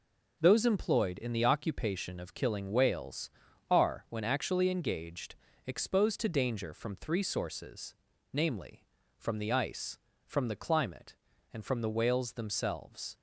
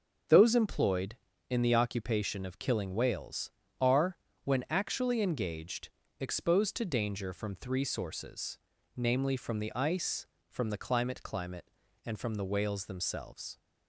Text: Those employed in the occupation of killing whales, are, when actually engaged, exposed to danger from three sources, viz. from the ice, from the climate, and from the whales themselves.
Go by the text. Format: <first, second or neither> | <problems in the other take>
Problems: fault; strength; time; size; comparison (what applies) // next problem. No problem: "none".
first | says "climate" twice; at 11.2 s